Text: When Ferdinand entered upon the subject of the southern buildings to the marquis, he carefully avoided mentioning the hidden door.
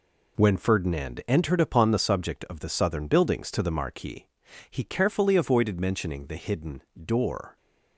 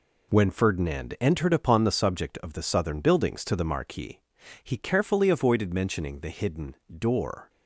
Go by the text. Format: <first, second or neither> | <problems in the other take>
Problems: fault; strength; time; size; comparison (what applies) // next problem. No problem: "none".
neither | pauses between "hidden" and "door"; slight; the same in both